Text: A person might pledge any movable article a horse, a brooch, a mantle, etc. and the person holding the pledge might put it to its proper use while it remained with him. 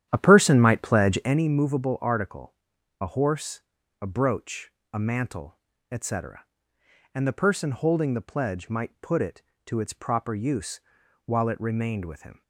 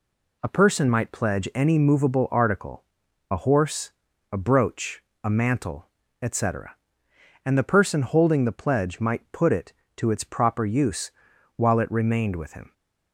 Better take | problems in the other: second | starts louder than the rest; strong; until 1.4 s; 10.5 dB // pauses between "article" and "a"; noticeable; at 2.5 s; 0.48 s long; noticeable in the second // pauses between "use" and "while"; at 10.8 s; 0.44 s long; also in the second

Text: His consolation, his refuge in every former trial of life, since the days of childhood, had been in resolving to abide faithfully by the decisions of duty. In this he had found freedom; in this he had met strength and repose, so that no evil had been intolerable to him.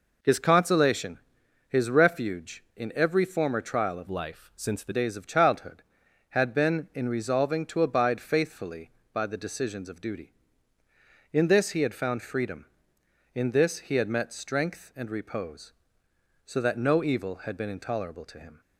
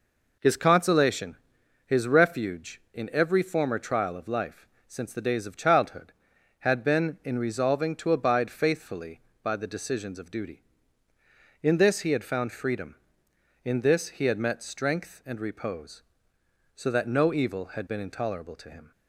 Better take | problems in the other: second | changes voice from "life" to "the"; from 4.0 to 4.9 s; 0.9 s long

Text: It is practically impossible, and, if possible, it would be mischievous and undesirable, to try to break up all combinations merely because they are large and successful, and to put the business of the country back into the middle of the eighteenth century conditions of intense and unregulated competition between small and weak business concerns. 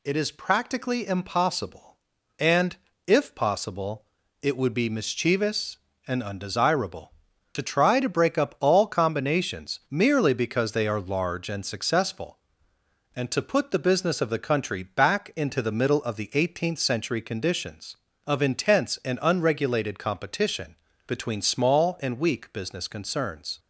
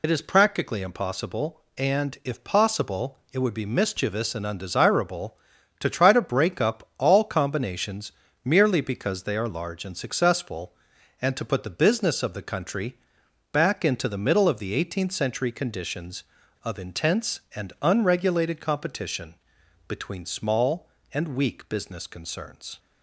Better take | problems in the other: first | loses the start of "It"; at 0.0 s; 60 ms // pauses between "combinations" and "merely"; slight; at 8.1 s; 0.32 s long // pauses between "country" and "back"; noticeable; at 12.9 s; 0.56 s long // pauses between "competition" and "between"; noticeable; at 19.3 s; 0.54 s long; slight in the first

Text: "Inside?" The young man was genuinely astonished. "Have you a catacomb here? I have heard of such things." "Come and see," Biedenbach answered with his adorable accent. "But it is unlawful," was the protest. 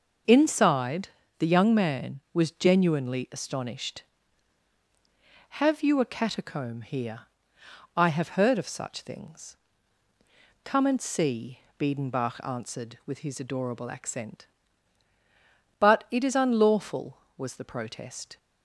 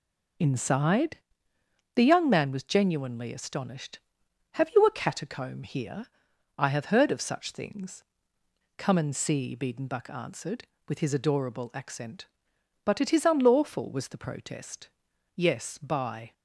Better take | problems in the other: first | goes on to say "Yes by"; noticeable; from 15.3 s on; 0.96 s long

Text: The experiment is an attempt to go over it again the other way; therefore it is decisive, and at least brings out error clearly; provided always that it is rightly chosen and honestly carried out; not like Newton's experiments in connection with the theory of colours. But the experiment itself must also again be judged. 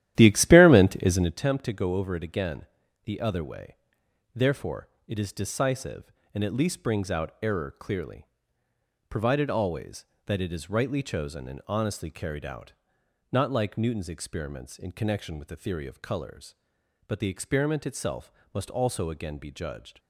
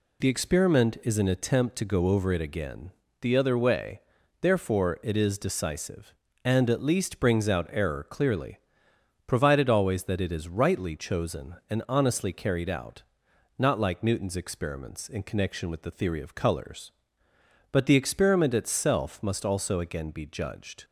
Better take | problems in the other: second | starts louder than the rest; strong; until 1.5 s; 12.5 dB // pauses between "again" and "the"; slight; at 2.6 s; 0.36 s long; slight in the second // pauses between "therefore" and "it"; slight; at 4.8 s; 0.20 s long // pauses between "itself" and "must"; slight; at 18.3 s; 0.22 s long

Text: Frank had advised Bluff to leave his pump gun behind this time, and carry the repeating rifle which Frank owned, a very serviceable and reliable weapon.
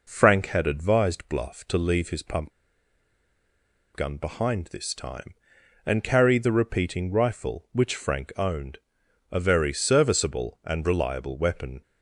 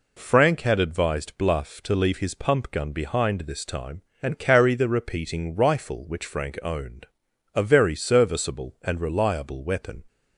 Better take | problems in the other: second | pauses between "pump" and "gun"; strong; at 2.5 s; 1.4 s long

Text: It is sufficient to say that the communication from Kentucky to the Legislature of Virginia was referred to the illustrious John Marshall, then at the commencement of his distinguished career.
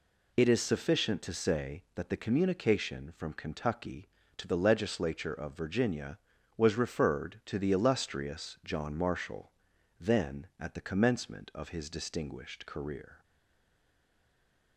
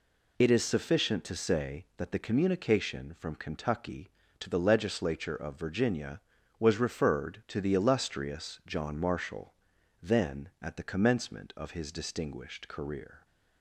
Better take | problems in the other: second | stays silent after the last word; noticeable; from 13.2 s on; 1.5 s long

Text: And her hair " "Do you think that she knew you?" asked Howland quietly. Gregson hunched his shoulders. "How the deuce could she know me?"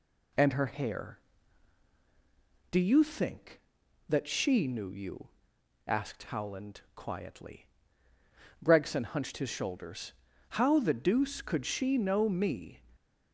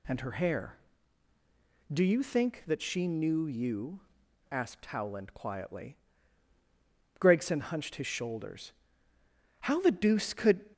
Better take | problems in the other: first | stops before "she know me"; at 10.7 s

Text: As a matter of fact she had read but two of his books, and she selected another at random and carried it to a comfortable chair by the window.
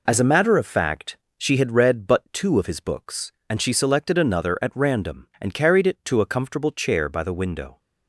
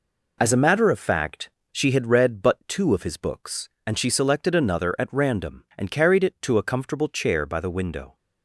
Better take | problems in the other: neither | pauses between "fact" and "she"; slight; the same in both

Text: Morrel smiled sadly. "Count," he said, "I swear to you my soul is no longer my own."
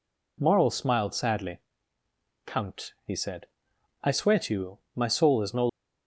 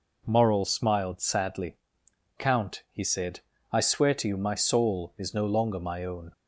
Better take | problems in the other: second | pauses between "you" and "my"; slight; at 4.7 s; 0.16 s long // stops before "longer my own"; at 5.6 s

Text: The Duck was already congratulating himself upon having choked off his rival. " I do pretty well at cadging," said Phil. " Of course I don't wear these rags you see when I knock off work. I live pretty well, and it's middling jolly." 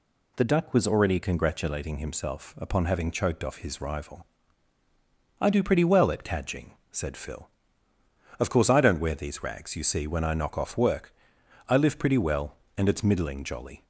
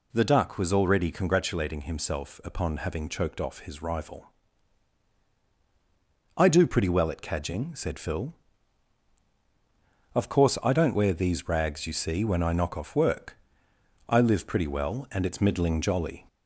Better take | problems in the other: first | gets louder; noticeable; throughout; 4 dB

